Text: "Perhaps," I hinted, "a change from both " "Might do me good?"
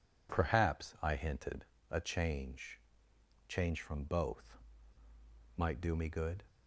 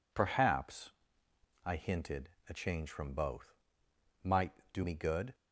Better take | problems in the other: second | says "change" twice; at 3.4 s

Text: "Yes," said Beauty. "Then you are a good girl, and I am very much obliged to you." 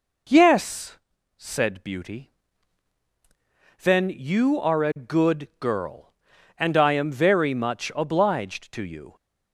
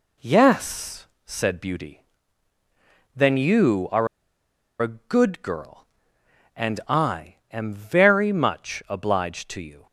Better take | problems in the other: first | pauses between "are" and "a"; noticeable; at 4.0 s; 0.74 s long // pauses between "I" and "am"; slight; at 7.3 s; 0.16 s long

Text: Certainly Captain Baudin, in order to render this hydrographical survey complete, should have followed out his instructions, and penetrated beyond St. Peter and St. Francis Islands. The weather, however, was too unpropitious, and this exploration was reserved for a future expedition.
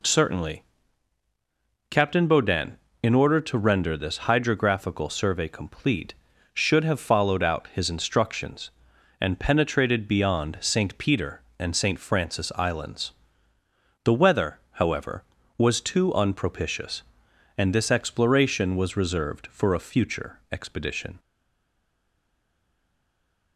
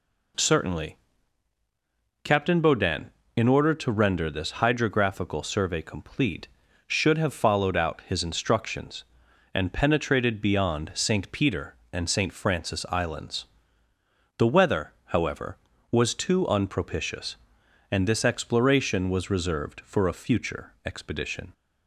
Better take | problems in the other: second | pauses between "Certainly" and "Captain"; strong; at 0.6 s; 1.2 s long; strong in the second // stays silent after the last word; from 21.1 s on; 2.4 s long

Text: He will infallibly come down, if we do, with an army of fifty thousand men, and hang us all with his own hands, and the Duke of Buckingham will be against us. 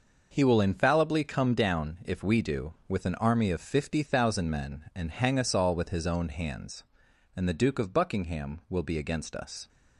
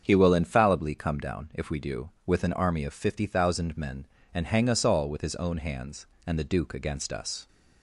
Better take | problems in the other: first | starts louder than the rest; strong; until 1.0 s; 7 dB // skips "of Buckingham will be"; at 6.7 s

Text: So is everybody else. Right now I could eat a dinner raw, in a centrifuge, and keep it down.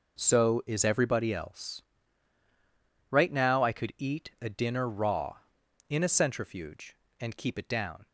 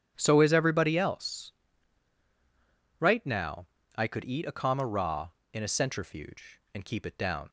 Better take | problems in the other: first | starts louder than the rest; strong; until 1.1 s; 9.5 dB // pauses between "now" and "I"; slight; at 3.6 s; 0.30 s long // says "comma" for "dinner"; at 4.5 s

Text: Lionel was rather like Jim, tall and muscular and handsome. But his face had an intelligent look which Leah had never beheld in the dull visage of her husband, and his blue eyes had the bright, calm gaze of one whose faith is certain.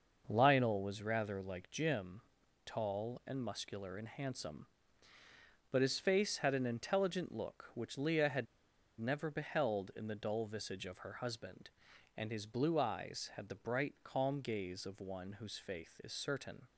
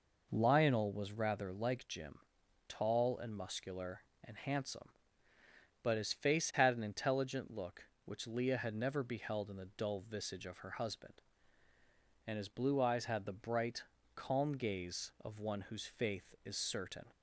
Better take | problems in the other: second | starts louder than the rest; noticeable; until 1.2 s; 6 dB // pauses between "had" and "never"; noticeable; at 8.4 s; 0.54 s long

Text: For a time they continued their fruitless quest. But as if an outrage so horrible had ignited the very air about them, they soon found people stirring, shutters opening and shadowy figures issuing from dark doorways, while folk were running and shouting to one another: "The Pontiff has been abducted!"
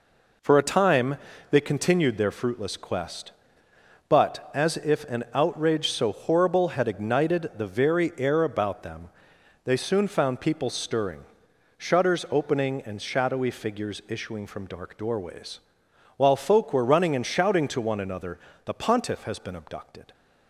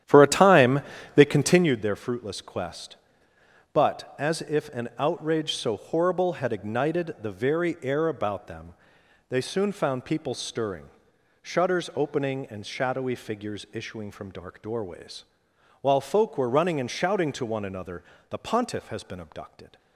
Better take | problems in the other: first | starts louder than the rest; strong; until 1.8 s; 10.5 dB // pauses between "time" and "they"; slight; at 0.8 s; 0.34 s long; slight in the first

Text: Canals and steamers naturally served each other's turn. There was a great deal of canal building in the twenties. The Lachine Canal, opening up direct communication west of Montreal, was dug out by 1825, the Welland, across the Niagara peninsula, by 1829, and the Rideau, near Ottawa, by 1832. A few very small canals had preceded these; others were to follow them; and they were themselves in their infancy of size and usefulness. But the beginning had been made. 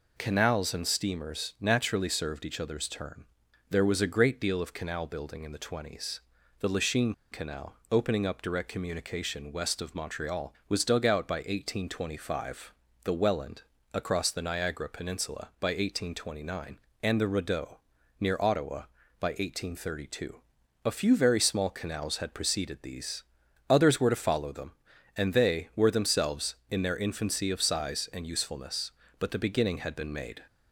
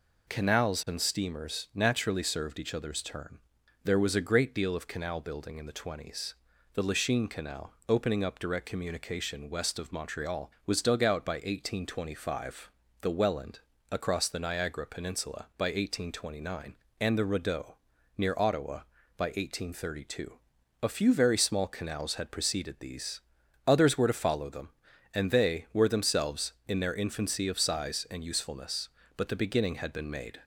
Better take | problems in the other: second | pauses between "Lachine" and "Canal"; slight; at 7.1 s; 0.19 s long

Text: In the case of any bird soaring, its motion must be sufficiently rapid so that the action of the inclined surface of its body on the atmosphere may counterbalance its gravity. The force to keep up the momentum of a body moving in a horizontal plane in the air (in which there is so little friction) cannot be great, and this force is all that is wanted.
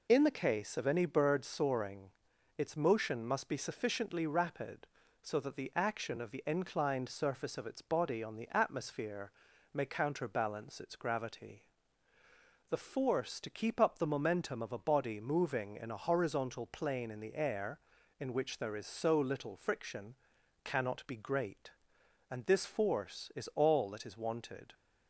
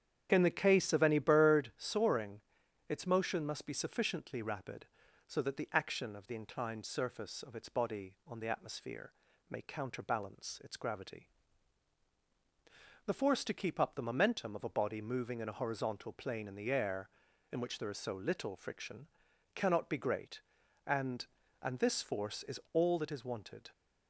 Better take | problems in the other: first | starts louder than the rest; strong; until 1.3 s; 9 dB // pauses between "atmosphere" and "may"; at 9.1 s; 0.38 s long; also in the first // says "and" twice; at 21.5 s

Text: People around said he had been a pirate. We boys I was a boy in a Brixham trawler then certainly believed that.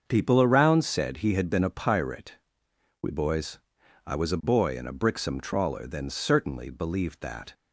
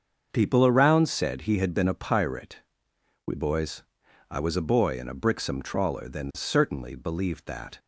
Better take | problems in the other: neither | starts louder than the rest; the same in both // pauses between "boys" and "I"; noticeable; the same in both

